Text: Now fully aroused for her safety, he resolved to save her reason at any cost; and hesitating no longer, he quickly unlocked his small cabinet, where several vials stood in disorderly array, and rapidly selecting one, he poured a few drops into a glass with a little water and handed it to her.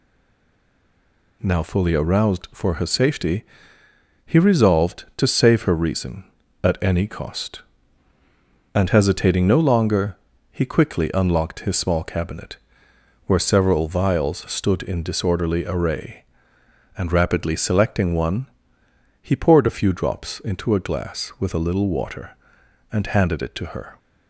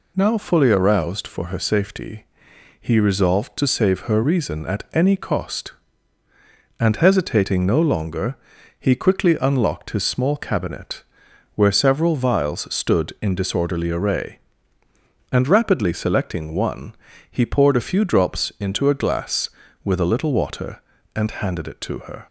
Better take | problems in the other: second | stays silent before the first word; noticeable; until 1.4 s; 1.4 s long

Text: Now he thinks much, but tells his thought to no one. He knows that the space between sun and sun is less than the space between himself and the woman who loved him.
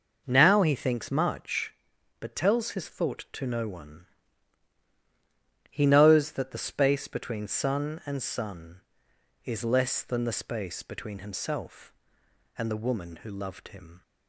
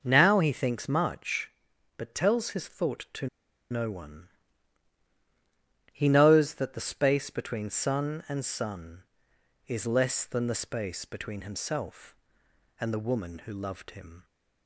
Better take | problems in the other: first | pauses between "to" and "no"; at 3.2 s; 0.44 s long

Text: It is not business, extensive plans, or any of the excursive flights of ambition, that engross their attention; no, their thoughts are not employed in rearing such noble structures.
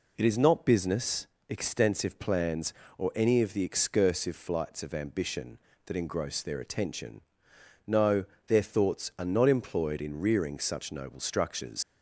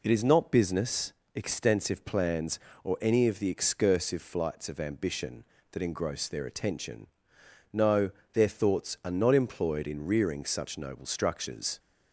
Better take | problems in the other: second | leaves "structures" unfinished; at 11.8 s; 100 ms

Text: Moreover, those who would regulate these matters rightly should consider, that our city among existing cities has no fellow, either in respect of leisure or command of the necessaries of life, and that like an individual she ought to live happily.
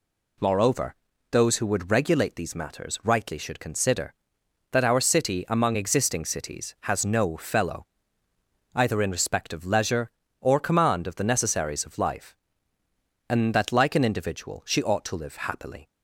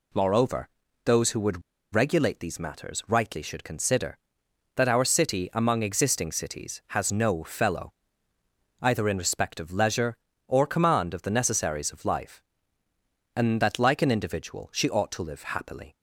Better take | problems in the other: first | pauses between "would" and "regulate"; slight; at 1.6 s; 0.33 s long

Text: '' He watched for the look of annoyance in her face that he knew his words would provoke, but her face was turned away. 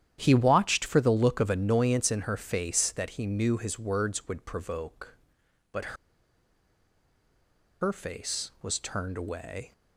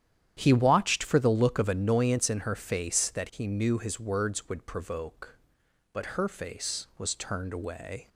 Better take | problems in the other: second | starts louder than the rest; strong; until 1.2 s; 10.5 dB; strong in the second // pauses between "but" and "her"; strong; at 5.9 s; 1.8 s long

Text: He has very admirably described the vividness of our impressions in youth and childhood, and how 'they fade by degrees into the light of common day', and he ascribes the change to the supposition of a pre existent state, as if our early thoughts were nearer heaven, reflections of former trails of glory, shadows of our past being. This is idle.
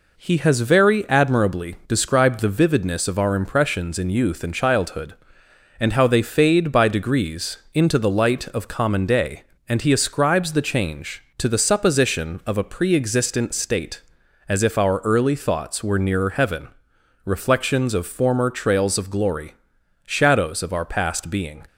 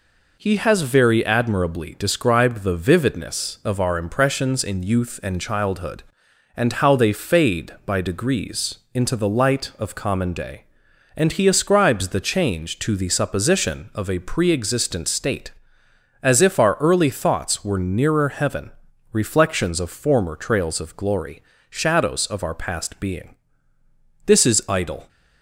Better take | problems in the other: second | pauses between "degrees" and "into"; slight; at 7.5 s; 0.16 s long; slight in the second // stops before "This is idle"; at 21.6 s

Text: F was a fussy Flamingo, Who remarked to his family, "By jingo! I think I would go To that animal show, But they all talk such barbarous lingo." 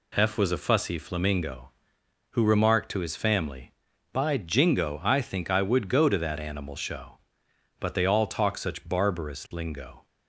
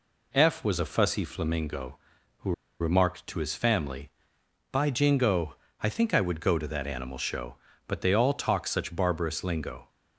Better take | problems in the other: first | pauses between "Who" and "remarked"; slight; at 2.5 s; 0.27 s long

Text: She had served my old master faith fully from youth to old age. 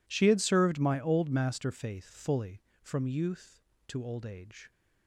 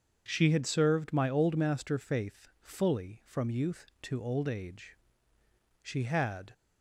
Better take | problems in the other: first | starts louder than the rest; until 1.2 s; 7 dB // goes on to say "She had"; noticeable; from 5.8 s on; 0.72 s long

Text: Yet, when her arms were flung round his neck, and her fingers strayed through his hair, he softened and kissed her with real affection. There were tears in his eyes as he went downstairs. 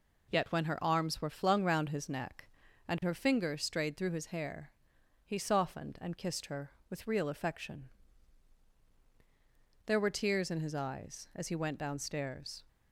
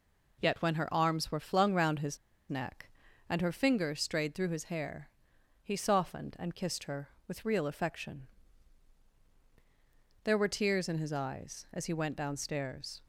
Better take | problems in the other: first | pauses between "his" and "neck"; slight; at 2.1 s; 0.31 s long

